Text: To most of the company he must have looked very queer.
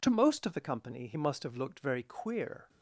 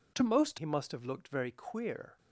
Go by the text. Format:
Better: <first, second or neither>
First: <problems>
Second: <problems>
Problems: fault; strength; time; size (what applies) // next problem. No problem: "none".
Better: first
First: none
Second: skips "of the company"; at 0.5 s